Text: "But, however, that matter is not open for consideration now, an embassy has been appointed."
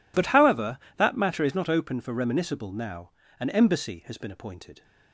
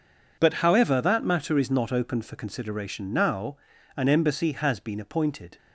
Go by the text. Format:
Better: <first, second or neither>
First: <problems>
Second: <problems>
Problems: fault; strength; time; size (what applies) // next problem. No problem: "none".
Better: second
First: says "reminiscible" for "consideration"; at 2.1 s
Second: none